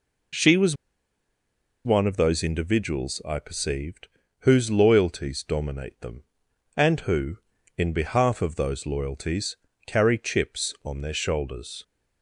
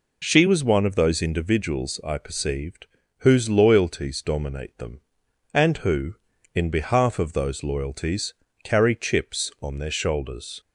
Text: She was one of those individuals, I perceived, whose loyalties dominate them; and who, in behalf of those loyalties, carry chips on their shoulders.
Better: second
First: pauses between "was" and "one"; at 0.7 s; 1.0 s long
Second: none

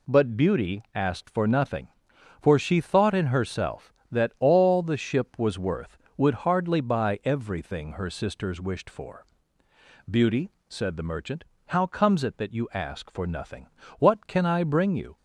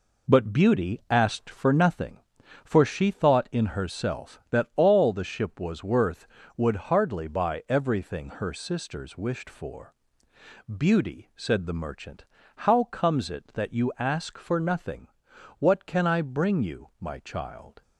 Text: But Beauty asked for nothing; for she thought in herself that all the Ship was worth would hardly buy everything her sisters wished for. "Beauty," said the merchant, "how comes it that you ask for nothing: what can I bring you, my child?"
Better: second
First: stops before "my child"; at 15.1 s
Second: none

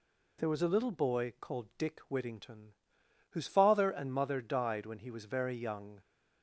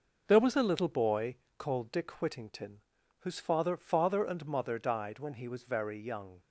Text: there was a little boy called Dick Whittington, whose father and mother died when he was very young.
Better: first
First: none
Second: pauses between "boy" and "called"; slight; at 1.3 s; 0.24 s long // says "father" twice; at 3.7 s

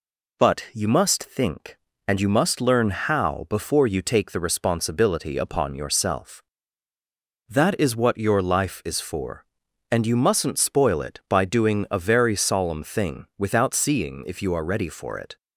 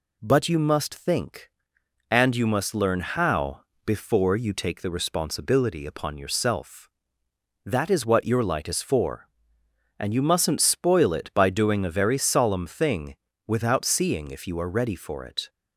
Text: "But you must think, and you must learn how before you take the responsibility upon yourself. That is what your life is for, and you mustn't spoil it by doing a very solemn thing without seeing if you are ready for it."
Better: first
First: none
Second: pauses between "how" and "before"; slight; at 3.6 s; 0.24 s long // says "light" for "life"; at 8.4 s // pauses between "thing" and "without"; slight; at 13.1 s; 0.32 s long

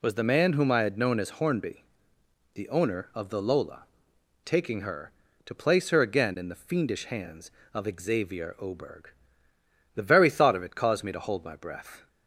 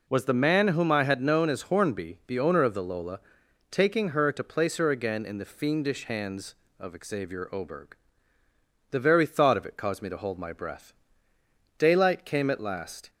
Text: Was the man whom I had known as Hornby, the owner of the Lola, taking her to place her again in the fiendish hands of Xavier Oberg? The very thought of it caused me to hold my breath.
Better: first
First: none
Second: goes on to say "Daylight came at last"; from 11.7 s on; 1.3 s long

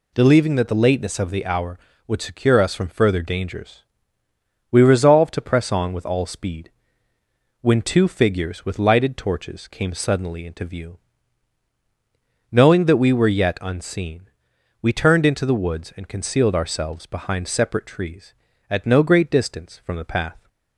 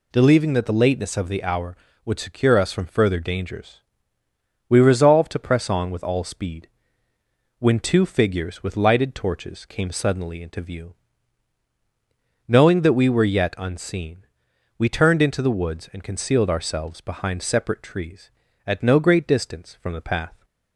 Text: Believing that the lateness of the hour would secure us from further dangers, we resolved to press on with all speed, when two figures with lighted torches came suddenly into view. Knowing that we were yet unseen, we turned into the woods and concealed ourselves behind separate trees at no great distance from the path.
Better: neither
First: none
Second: none

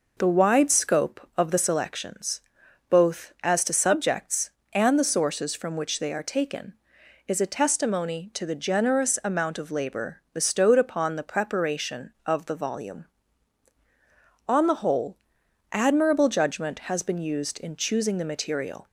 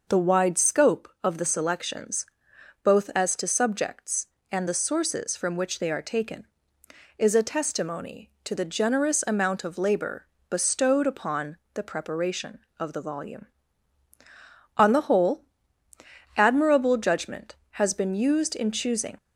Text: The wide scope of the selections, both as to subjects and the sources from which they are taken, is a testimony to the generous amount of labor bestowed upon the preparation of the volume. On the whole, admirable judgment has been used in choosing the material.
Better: first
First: none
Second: pauses between "labor" and "bestowed"; slight; at 10.2 s; 0.24 s long // pauses between "upon" and "the"; slight; at 11.5 s; 0.16 s long // stops before "the material"; at 19.1 s

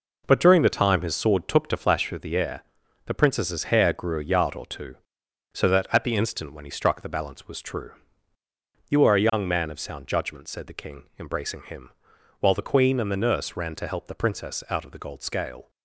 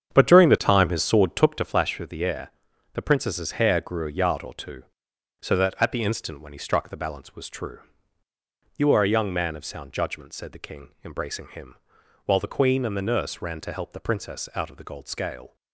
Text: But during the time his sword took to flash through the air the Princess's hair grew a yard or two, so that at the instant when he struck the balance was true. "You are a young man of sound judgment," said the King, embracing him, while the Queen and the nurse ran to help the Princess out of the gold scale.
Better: first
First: pauses between "air" and "the"; at 2.6 s; 0.42 s long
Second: starts louder than the rest; strong; until 1.7 s; 8 dB // pauses between "air" and "the"; at 2.5 s; 0.42 s long

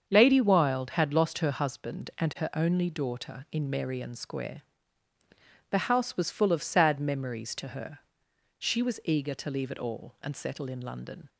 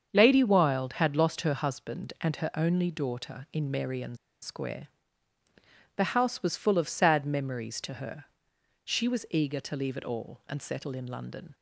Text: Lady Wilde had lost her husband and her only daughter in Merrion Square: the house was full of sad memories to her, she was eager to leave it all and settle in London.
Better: first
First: starts louder than the rest; strong; until 1.0 s; 7 dB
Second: starts louder than the rest; strong; until 1.1 s; 7 dB // pauses between "Merrion" and "Square"; slight; at 4.1 s; 0.26 s long

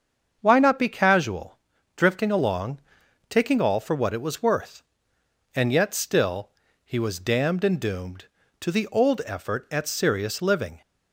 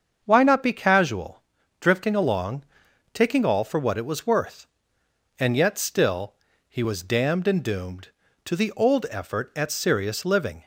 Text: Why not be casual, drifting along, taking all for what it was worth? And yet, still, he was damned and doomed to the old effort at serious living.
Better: neither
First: starts louder than the rest; until 1.4 s; 7 dB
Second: starts louder than the rest; until 1.2 s; 7 dB

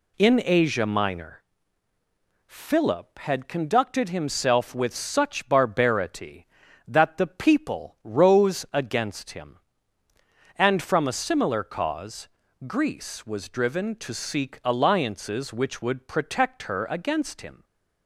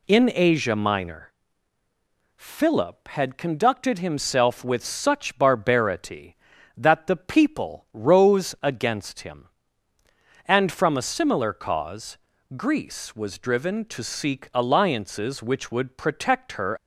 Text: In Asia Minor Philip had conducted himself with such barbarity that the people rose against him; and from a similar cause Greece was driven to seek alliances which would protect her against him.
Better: first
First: pauses between "Minor" and "Philip"; at 1.4 s; 1.0 s long // pauses between "cause" and "Greece"; at 12.2 s; 0.40 s long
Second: pauses between "Minor" and "Philip"; at 1.3 s; 1.0 s long // pauses between "cause" and "Greece"; at 12.1 s; 0.40 s long // stops before "against him"; at 16.7 s

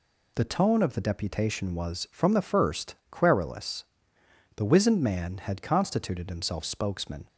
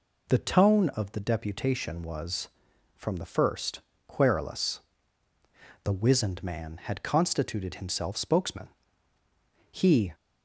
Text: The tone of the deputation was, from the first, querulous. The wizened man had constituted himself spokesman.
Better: first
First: none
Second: goes on to say "He"; slight; from 9.7 s on; 0.42 s long

